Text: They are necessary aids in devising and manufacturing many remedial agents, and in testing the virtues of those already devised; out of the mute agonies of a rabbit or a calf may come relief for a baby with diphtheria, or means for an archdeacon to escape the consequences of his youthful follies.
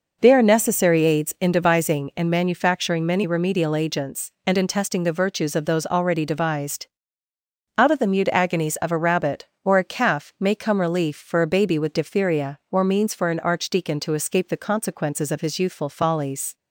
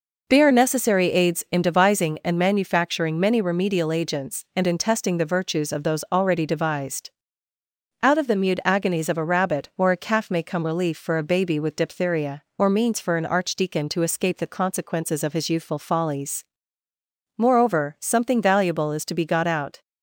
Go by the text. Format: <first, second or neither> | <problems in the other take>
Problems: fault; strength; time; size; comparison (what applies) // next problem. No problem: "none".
first | goes on to say "Moreover something valuable is to be got out"; strong; from 17.3 s on; 2.4 s long